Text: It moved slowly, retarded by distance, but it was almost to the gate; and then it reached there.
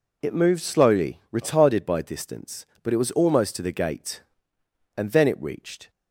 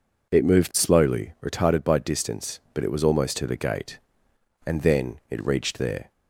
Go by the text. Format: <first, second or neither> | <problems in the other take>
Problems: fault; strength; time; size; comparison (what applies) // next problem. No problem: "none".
second | stops before "there"; at 5.8 s